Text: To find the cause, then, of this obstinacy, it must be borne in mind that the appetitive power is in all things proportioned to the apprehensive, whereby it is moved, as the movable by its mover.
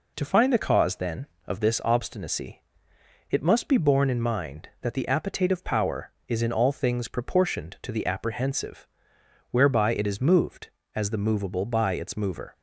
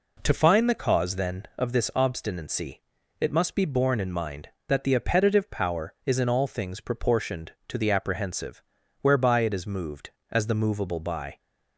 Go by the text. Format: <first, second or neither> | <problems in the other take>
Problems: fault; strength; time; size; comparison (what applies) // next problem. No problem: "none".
first | stops before "its mover"; at 11.3 s